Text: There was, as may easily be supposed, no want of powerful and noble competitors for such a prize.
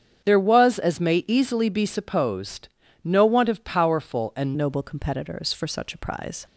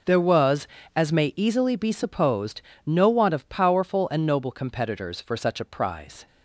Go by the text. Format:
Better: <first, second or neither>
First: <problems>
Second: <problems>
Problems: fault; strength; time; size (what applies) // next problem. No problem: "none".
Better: second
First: starts louder than the rest; strong; until 1.2 s; 8 dB // changes voice at "noble"; from 4.5 s on; 1.9 s long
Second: none